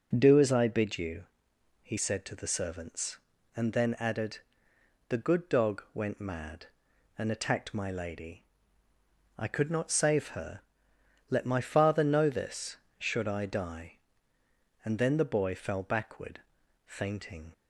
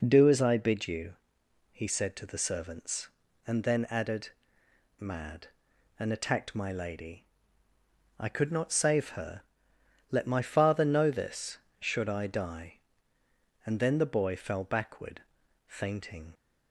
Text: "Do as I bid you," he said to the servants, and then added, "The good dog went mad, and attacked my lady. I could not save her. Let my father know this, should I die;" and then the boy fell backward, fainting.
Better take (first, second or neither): first